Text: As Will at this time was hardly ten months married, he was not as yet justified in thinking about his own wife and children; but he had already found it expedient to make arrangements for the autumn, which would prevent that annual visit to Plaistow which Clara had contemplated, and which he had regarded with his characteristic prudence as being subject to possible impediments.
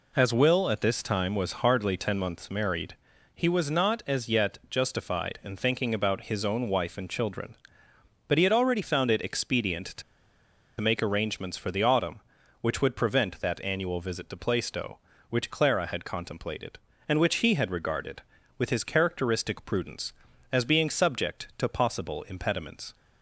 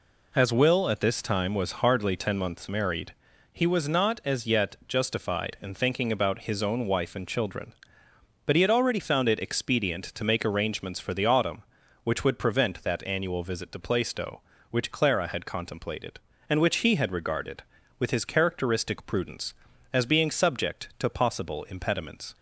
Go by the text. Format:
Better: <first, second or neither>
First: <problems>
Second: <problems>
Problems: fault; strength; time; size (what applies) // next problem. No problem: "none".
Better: second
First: pauses between "to" and "make"; noticeable; at 10.0 s; 0.78 s long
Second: none